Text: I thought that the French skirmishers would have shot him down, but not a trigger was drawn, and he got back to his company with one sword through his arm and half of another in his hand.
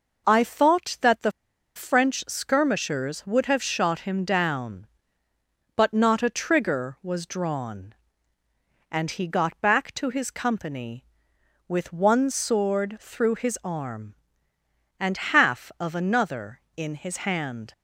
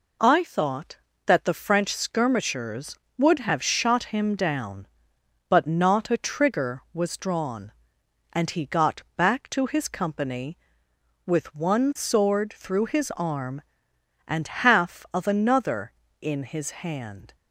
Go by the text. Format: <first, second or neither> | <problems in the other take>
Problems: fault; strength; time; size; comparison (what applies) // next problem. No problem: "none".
second | pauses between "the" and "French"; at 1.3 s; 0.44 s long